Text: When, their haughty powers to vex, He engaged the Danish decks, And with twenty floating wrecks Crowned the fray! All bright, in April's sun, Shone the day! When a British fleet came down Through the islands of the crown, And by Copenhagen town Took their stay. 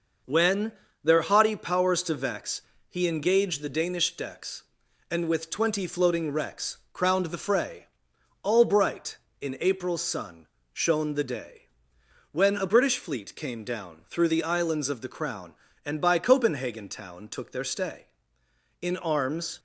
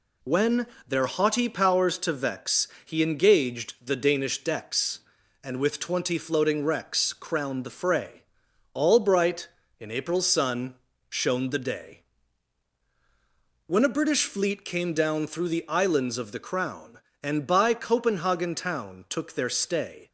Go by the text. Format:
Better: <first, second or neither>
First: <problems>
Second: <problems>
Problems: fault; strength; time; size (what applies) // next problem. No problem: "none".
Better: second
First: pauses between "wrecks" and "Crowned"; slight; at 6.7 s; 0.16 s long // goes on to say "In arms"; noticeable; from 18.8 s on; 0.78 s long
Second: none